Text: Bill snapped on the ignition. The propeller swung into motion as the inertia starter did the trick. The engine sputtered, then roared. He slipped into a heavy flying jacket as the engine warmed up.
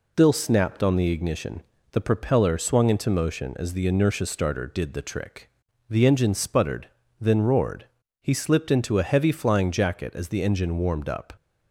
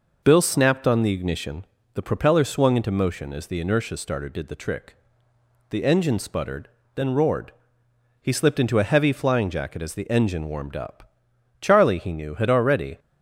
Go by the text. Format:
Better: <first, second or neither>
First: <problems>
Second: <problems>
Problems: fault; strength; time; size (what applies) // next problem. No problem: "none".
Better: first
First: none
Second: goes on to say "Charlie he knew had already"; from 11.6 s on; 1.3 s long